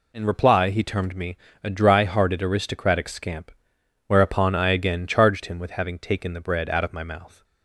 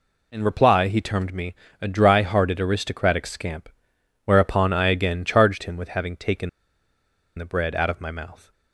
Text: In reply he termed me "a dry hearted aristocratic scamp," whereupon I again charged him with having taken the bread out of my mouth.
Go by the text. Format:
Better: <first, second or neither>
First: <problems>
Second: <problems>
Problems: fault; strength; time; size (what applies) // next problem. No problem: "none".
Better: first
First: pauses between "me" and "a"; slight; at 1.3 s; 0.26 s long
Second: pauses between "me" and "a"; slight; at 1.5 s; 0.26 s long // pauses between "taken" and "the"; noticeable; at 6.4 s; 0.87 s long